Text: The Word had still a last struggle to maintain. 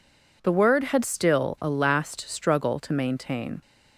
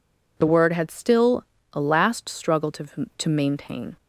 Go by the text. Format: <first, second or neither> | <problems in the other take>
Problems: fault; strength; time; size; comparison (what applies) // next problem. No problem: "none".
first | pauses between "still" and "a"; slight; at 1.4 s; 0.28 s long // says "to" twice; at 3.1 s